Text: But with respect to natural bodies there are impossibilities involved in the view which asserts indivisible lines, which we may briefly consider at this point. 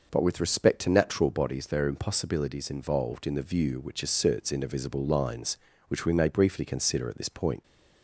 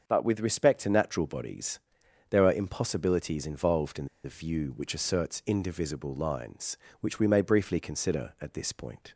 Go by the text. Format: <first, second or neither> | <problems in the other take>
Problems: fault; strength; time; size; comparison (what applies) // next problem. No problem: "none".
first | starts louder than the rest; until 1.0 s; 6.5 dB // pauses between "bodies" and "there"; noticeable; at 1.7 s; 0.52 s long // pauses between "in" and "the"; slight; at 4.0 s; 0.18 s long